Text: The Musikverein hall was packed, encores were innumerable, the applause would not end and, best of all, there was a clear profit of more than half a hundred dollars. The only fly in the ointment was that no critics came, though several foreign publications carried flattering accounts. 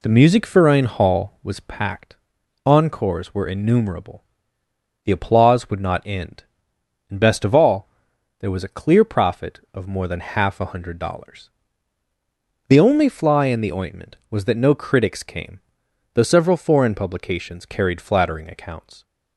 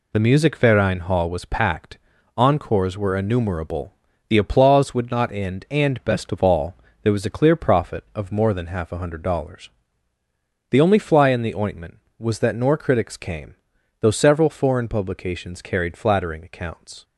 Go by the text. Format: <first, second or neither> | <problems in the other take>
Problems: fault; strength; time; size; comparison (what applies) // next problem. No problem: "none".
first | says "nor" for "no"; at 12.5 s